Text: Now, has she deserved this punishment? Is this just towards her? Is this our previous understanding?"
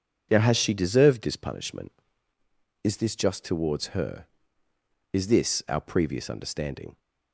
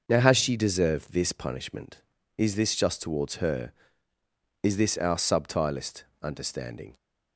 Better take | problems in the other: first | starts louder than the rest; noticeable; until 1.0 s; 6 dB // says "subtilist" for "previous"; at 5.1 s

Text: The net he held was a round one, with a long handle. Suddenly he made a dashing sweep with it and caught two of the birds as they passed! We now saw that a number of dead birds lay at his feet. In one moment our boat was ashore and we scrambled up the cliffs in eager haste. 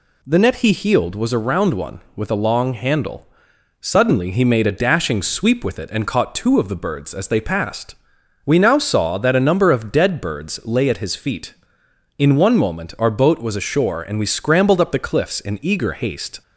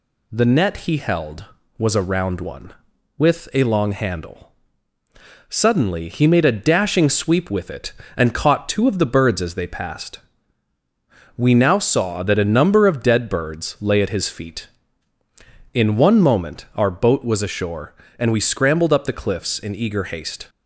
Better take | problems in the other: second | says "healed" for "held"; at 0.7 s

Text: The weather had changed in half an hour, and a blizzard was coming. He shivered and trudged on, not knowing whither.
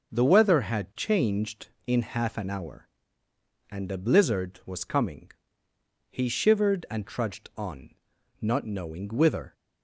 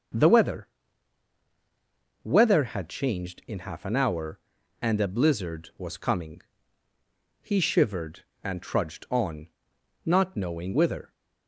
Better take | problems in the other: first | starts louder than the rest; until 2.7 s; 6.5 dB // says "weather" twice; at 2.2 s

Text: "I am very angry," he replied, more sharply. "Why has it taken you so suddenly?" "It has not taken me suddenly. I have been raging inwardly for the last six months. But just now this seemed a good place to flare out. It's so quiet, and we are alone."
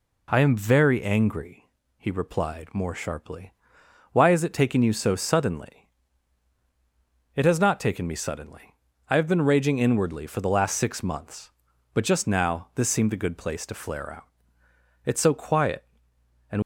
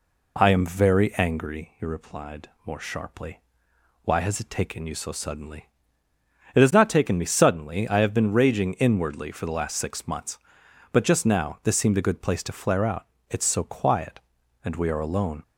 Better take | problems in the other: second | stops before "we are alone"; at 16.6 s

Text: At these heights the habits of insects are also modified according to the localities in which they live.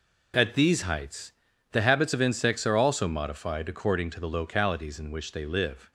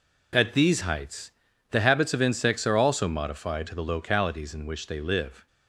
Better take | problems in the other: first | pauses between "heights" and "the"; at 1.2 s; 0.40 s long; also in the first // skips "according"; at 3.6 s

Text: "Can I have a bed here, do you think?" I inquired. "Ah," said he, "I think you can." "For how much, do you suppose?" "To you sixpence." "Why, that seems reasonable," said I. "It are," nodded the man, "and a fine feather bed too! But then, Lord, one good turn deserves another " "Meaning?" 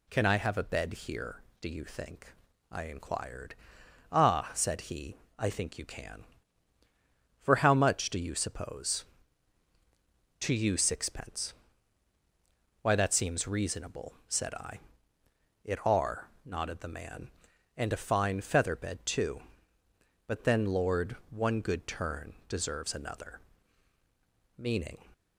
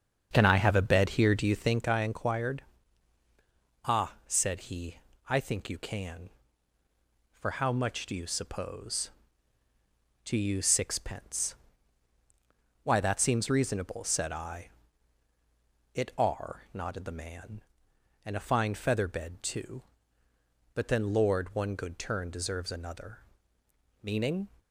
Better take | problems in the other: first | starts louder than the rest; strong; until 1.9 s; 7.5 dB

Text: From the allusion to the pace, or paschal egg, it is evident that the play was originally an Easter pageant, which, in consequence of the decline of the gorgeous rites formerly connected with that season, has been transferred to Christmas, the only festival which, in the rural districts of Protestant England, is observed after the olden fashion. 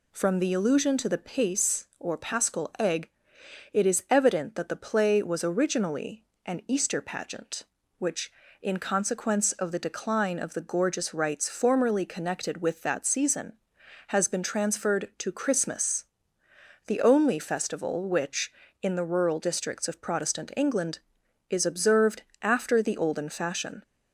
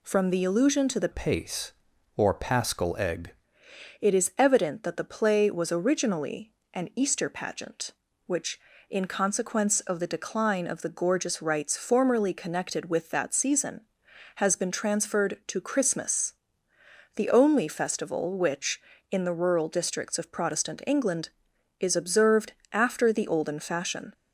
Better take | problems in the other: first | changes voice from "pace" to "egg"; from 1.1 to 3.3 s; 2.2 s long // pauses between "originally" and "an"; slight; at 6.5 s; 0.20 s long; slight in the first // pauses between "observed" and "after"; slight; at 22.5 s; 0.18 s long; slight in the first

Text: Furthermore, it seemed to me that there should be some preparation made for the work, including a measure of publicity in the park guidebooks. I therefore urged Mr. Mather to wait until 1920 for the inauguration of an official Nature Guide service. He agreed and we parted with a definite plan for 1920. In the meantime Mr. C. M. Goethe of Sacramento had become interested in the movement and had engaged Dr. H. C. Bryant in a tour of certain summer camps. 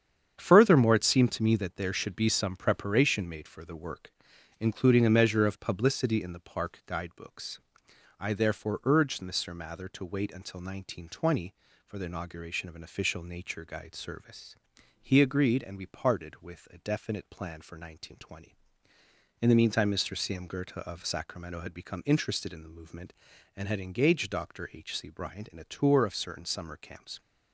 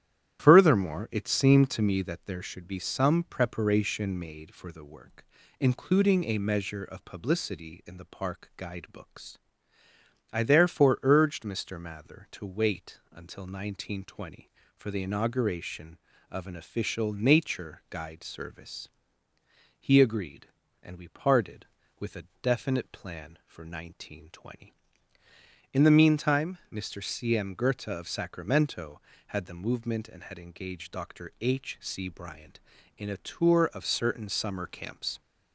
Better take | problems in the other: first | starts louder than the rest; strong; until 1.4 s; 11.5 dB; strong in the first // pauses between "a" and "definite"; slight; at 22.2 s; 0.16 s long // skips "become interested in"; at 29.4 s

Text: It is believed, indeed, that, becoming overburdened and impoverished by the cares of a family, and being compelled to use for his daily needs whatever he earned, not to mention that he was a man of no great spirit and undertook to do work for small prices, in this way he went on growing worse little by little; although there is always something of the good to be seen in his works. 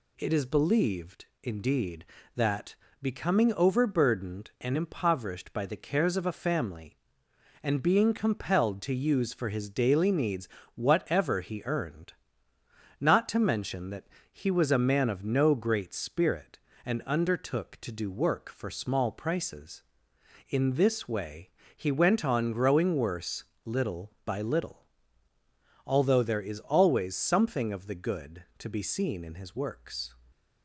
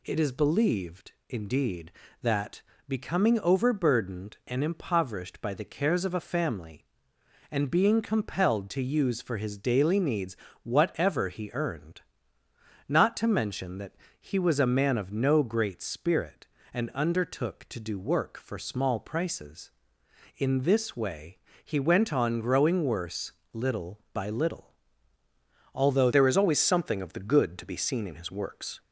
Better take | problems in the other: first | pauses between "needs" and "whatever"; slight; at 10.3 s; 0.28 s long; slight in the first // pauses between "that" and "he"; slight; at 13.9 s; 0.26 s long; slight in the first // pauses between "way" and "he"; slight; at 21.3 s; 0.26 s long; slight in the first // pauses between "worse" and "little"; slight; at 23.3 s; 0.22 s long; slight in the first // changes voice at "there"; from 26.1 s on; 2.7 s long

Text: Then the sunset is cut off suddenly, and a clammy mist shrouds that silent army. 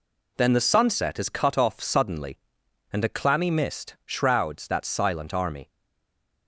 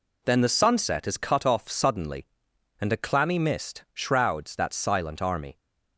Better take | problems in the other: second | stays silent after the last word; slight; from 5.6 s on; 0.8 s long

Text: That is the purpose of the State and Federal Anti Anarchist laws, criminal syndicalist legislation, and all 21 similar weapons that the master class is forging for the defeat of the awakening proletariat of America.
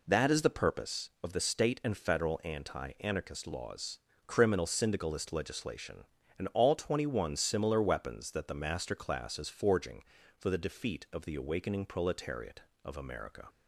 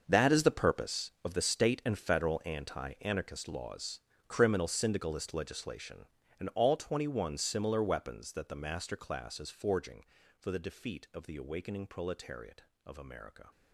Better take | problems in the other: first | gets quieter; strong; throughout; 13.5 dB

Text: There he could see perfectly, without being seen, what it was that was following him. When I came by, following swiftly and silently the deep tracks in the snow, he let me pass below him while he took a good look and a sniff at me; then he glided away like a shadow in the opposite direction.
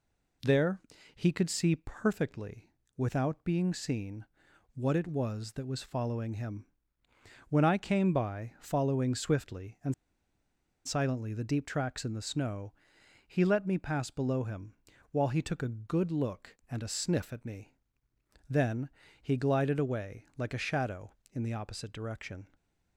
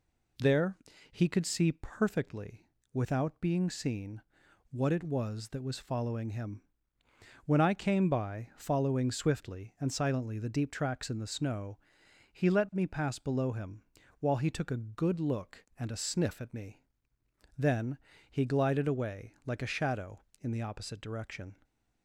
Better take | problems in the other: second | pauses between "There" and "he"; slight; at 0.7 s; 0.34 s long; slight in the second // pauses between "and" and "silently"; noticeable; at 9.9 s; 0.92 s long // pauses between "him" and "while"; at 14.7 s; 0.38 s long; also in the second // pauses between "then" and "he"; slight; at 18.8 s; 0.34 s long; slight in the second // stays silent after the last word; slight; from 22.4 s on; 0.5 s long

